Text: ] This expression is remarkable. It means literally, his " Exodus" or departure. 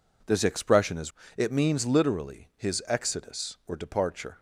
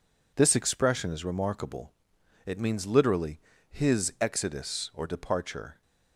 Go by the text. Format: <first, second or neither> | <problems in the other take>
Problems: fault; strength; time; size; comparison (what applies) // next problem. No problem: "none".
second | skips "remarkable"; at 1.2 s